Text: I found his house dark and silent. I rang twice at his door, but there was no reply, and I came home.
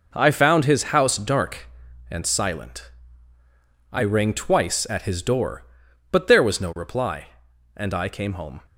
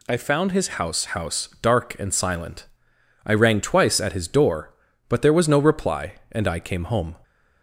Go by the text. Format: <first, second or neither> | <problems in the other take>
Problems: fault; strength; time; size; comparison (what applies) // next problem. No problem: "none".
first | says "house" twice; at 1.0 s